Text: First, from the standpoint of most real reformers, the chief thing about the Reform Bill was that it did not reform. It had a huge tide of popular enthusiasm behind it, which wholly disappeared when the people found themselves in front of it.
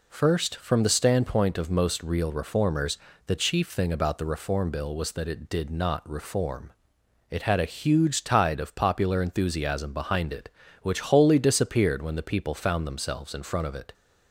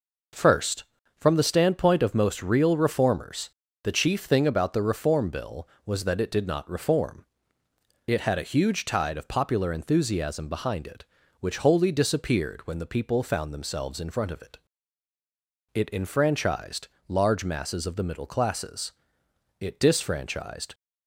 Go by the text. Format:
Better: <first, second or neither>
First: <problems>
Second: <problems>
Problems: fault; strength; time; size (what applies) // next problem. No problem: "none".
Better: first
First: none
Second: goes on to say "It enfranchised large masses of the middle classes it disfranchised"; strong; from 15.7 s on; 5.0 s long